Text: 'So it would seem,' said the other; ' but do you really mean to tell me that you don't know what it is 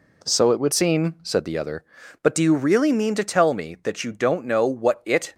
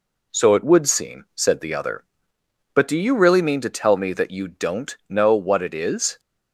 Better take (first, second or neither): second